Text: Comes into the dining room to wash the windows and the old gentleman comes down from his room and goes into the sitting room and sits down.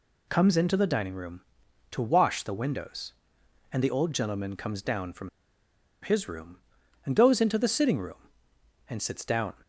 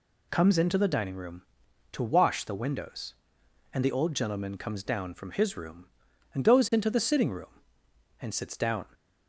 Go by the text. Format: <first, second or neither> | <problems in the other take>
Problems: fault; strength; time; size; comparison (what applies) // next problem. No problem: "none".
second | pauses between "from" and "his"; noticeable; at 5.2 s; 0.74 s long